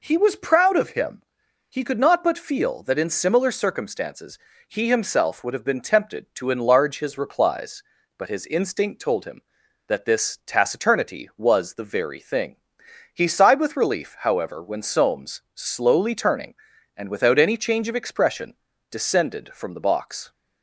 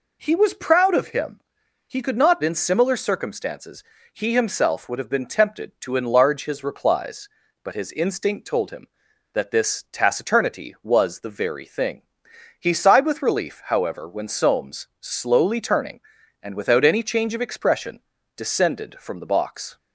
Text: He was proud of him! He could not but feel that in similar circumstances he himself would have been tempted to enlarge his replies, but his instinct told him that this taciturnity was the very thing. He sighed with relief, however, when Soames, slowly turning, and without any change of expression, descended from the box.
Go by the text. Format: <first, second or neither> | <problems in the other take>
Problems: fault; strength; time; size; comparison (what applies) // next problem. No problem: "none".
first | skips "but feel that"; at 2.4 s // pauses between "circumstances" and "he"; slight; at 3.8 s; 0.32 s long; slight in the first